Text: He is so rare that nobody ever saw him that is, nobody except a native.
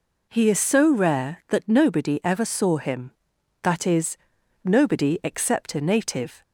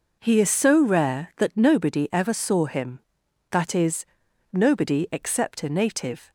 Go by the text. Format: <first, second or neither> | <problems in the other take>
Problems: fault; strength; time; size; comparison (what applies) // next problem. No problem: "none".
first | gets quieter; strong; throughout; 11.5 dB